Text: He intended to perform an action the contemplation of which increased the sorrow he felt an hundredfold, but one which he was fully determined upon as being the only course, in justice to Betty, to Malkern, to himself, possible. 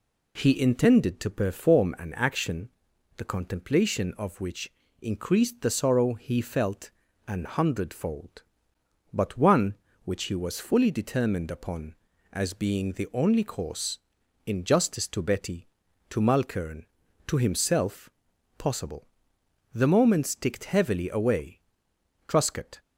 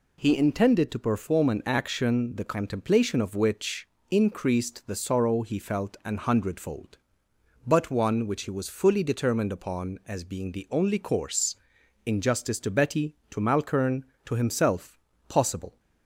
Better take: second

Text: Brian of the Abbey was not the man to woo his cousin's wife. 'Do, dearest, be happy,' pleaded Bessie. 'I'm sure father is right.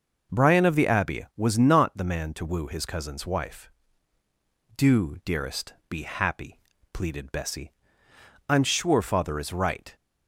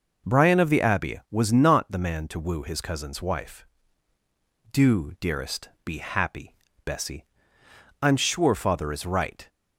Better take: first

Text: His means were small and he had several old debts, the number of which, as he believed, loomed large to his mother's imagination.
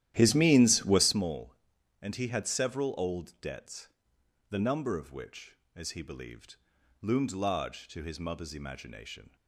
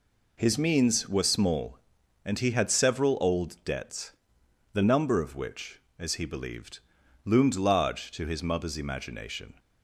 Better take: second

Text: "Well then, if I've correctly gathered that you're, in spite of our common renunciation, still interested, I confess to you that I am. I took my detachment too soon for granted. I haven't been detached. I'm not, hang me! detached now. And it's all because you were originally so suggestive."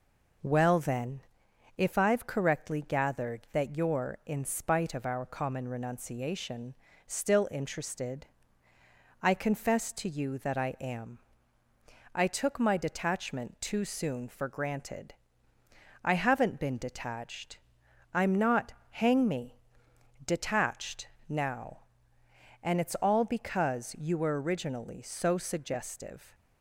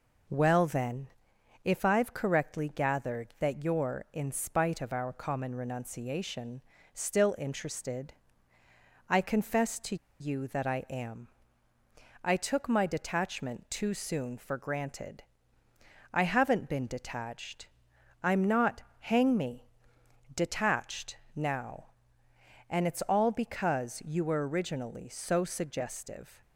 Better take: first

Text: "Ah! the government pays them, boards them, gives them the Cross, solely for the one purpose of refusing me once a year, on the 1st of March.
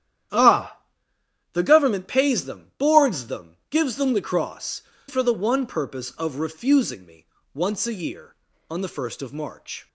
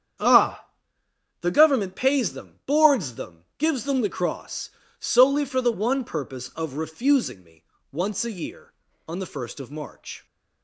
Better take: second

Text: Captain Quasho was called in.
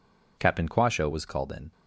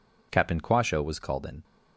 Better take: neither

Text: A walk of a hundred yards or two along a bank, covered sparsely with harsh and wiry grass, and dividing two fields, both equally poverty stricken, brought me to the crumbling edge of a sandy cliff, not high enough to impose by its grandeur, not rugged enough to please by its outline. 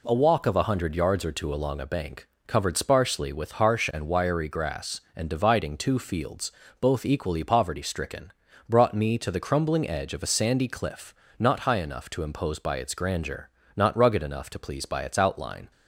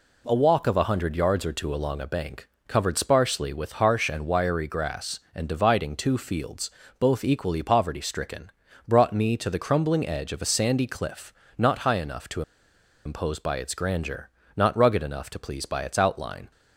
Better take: first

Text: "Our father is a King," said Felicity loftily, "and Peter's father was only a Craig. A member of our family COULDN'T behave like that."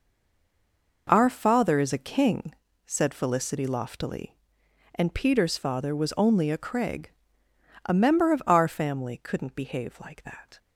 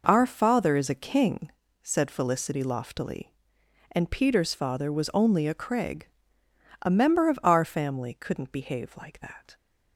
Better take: second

